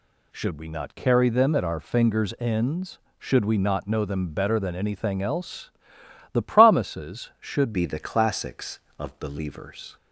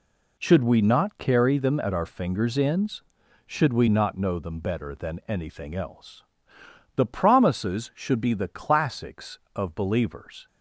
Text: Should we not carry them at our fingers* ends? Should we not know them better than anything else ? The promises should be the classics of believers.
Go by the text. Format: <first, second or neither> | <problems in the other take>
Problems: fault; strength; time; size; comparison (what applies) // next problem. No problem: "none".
second | changes voice at "be"; from 7.7 s on; 2.2 s long